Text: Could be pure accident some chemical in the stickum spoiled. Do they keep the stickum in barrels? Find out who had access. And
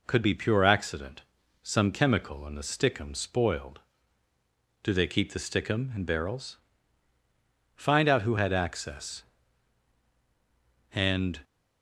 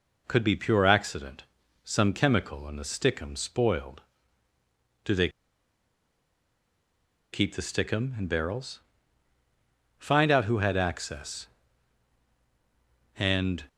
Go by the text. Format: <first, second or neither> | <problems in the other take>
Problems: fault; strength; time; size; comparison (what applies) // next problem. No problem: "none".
first | pauses between "accident" and "some"; at 1.4 s; 0.42 s long; also in the first // pauses between "they" and "keep"; strong; at 5.2 s; 2.0 s long